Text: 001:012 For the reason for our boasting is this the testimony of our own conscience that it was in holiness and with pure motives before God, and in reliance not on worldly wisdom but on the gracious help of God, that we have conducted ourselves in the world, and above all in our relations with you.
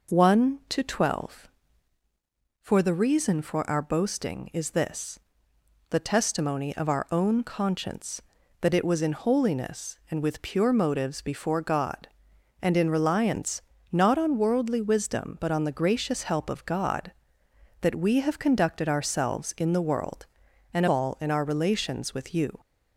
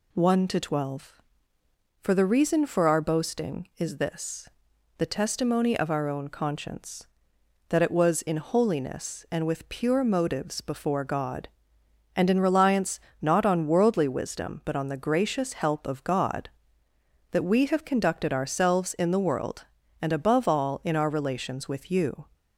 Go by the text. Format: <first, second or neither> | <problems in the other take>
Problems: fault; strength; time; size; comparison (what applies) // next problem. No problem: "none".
second | pauses between "this" and "the"; noticeable; at 5.1 s; 0.70 s long; noticeable in the second // pauses between "reliance" and "not"; slight; at 13.6 s; 0.30 s long; slight in the second // skips "above"; at 20.8 s